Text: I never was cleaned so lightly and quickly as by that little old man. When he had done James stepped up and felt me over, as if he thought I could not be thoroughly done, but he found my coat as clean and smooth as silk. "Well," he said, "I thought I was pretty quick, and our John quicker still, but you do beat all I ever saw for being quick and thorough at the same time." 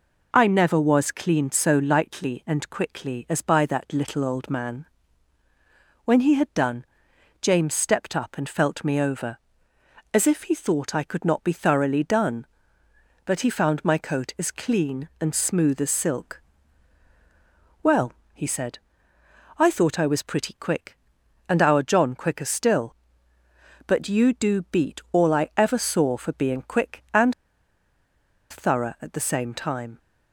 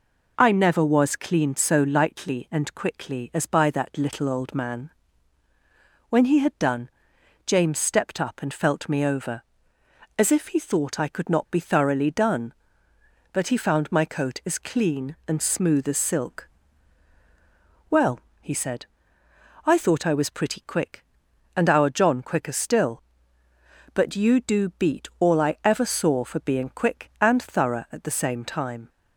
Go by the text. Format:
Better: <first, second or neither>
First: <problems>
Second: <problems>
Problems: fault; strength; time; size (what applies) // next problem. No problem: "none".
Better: second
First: pauses between "done" and "James"; noticeable; at 6.8 s; 0.56 s long // pauses between "and" and "thorough"; at 27.3 s; 1.1 s long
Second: pauses between "done" and "James"; noticeable; at 6.8 s; 0.56 s long